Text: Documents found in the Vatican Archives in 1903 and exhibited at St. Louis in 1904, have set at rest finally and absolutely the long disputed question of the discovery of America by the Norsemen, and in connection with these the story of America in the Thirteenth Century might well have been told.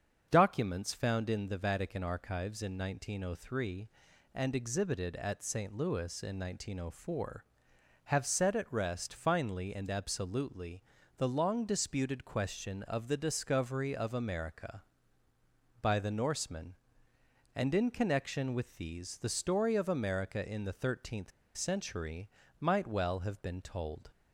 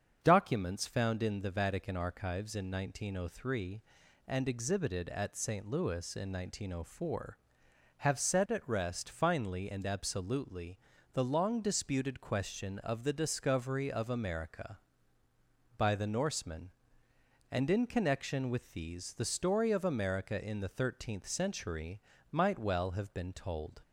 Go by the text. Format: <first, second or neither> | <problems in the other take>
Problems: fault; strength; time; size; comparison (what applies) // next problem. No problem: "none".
second | starts louder than the rest; until 1.3 s; 7 dB; also in the second // pauses between "absolutely" and "the"; slight; at 10.8 s; 0.34 s long; slight in the second // pauses between "Thirteenth" and "Century"; slight; at 21.3 s; 0.25 s long // pauses between "Century" and "might"; slight; at 22.2 s; 0.32 s long; slight in the second